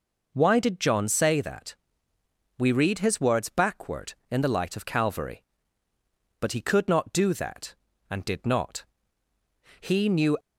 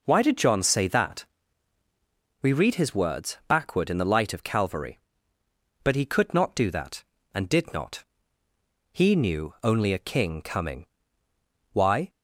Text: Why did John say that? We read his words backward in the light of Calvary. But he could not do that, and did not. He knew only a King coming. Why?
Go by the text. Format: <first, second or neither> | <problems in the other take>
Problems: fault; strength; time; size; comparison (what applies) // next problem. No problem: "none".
second | stops before "only a King coming Why"; at 10.3 s